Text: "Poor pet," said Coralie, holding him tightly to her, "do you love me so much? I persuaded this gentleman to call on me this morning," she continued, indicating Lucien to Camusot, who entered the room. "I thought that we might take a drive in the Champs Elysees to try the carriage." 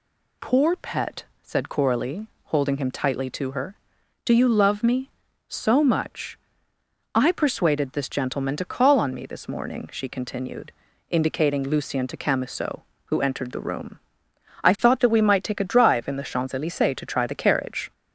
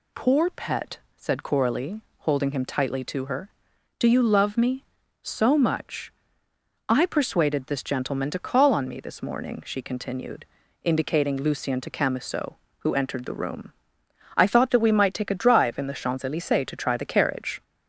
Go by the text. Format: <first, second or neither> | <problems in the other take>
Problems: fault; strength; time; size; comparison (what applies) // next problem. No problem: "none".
neither | none